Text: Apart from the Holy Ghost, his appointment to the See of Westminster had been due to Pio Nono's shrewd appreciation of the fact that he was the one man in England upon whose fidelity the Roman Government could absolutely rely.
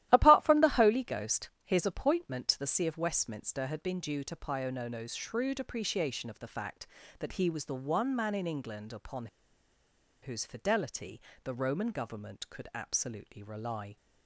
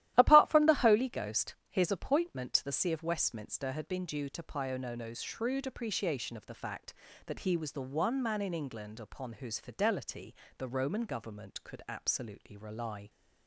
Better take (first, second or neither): second